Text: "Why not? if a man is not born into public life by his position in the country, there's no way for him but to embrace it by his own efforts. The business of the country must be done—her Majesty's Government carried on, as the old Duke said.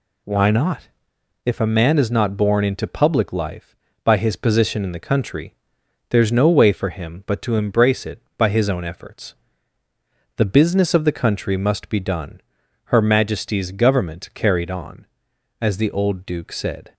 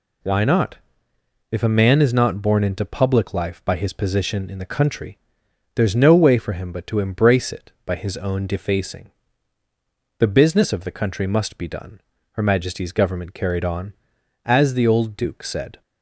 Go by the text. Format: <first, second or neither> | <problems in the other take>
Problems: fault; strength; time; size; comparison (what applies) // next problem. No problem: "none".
first | says "defacing" for "efforts"; at 8.4 s